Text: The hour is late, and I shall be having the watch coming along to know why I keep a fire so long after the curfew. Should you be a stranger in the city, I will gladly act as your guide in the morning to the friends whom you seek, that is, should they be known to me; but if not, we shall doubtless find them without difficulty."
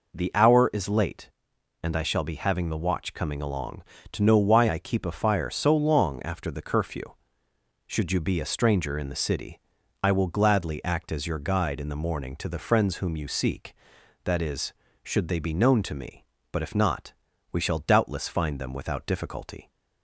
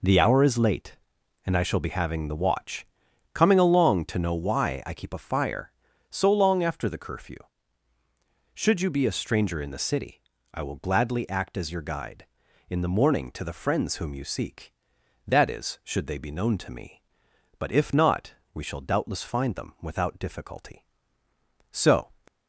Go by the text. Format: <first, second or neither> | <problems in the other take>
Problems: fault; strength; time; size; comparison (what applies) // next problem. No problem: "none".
first | pauses between "watch" and "coming"; noticeable; at 2.8 s; 0.49 s long // goes on to say "So"; slight; from 21.7 s on; 0.38 s long